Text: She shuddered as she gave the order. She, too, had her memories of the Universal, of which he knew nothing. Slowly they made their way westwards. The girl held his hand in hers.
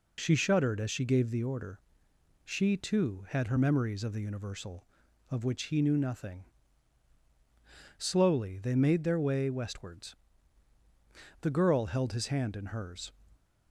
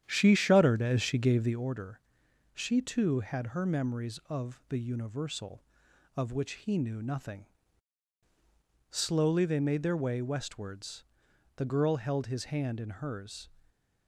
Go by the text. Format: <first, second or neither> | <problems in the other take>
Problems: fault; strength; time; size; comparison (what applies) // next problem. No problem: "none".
first | starts louder than the rest; strong; until 1.7 s; 9.5 dB